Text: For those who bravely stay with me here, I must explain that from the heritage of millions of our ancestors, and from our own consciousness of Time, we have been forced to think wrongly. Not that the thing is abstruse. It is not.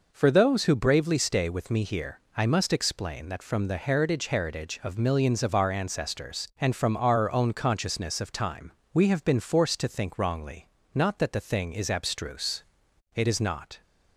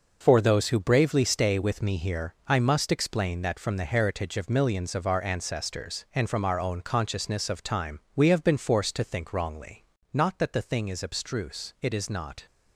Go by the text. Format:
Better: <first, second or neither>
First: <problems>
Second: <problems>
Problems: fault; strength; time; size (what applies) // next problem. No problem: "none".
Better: second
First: says "heritage" twice; at 4.2 s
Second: none